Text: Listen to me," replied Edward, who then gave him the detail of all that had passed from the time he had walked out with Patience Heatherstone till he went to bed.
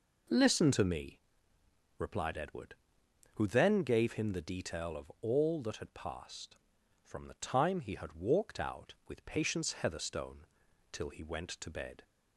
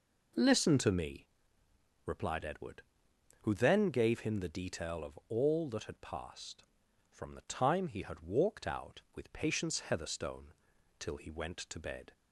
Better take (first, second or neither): neither